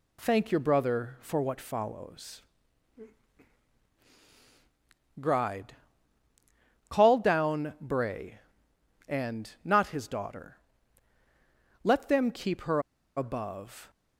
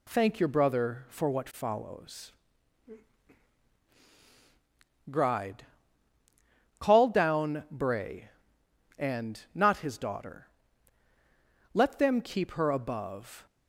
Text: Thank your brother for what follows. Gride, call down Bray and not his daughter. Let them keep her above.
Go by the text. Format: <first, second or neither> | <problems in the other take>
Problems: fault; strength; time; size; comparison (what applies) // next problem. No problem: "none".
second | pauses between "her" and "above"; slight; at 12.8 s; 0.35 s long